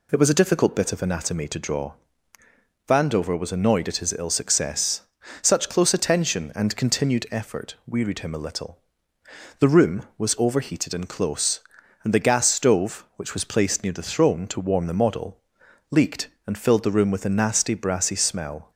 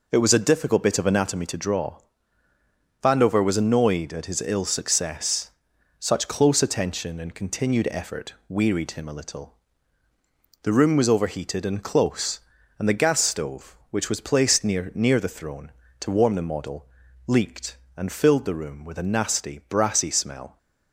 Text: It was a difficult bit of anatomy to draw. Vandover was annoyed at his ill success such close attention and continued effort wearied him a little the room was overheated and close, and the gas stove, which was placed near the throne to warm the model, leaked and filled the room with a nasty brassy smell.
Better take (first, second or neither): first